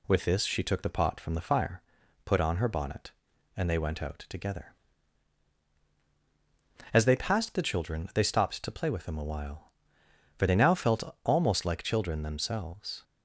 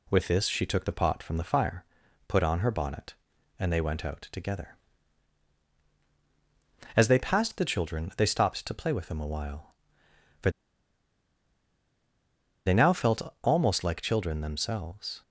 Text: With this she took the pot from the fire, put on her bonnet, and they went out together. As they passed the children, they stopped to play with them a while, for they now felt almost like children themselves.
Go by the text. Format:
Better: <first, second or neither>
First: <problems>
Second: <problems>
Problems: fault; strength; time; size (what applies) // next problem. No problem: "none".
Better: first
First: none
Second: pauses between "for" and "they"; strong; at 10.4 s; 2.1 s long